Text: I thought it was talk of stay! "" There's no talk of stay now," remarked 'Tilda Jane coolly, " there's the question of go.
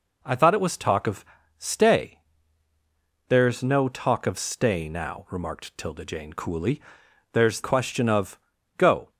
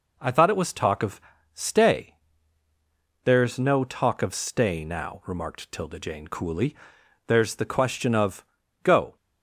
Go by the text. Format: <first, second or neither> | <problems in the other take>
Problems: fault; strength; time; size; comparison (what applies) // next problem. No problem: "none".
second | pauses between "of" and "stay"; slight; at 1.2 s; 0.32 s long; slight in the second // skips "the"; at 7.6 s // pauses between "of" and "go"; slight; at 8.3 s; 0.36 s long; slight in the second